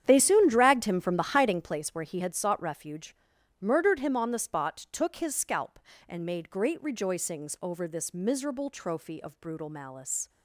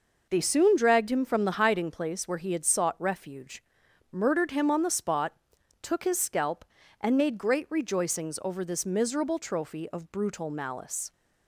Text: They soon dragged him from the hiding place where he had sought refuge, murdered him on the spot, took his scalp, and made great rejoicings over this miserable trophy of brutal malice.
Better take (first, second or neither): second